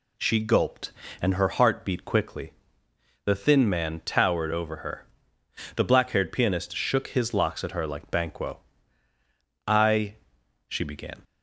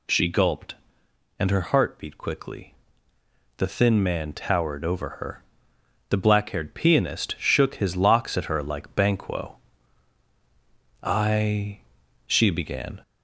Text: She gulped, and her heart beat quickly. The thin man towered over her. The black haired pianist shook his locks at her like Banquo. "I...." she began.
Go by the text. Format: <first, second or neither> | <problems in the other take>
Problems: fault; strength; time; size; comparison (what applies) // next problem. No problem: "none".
first | gets louder; slight; throughout; 2 dB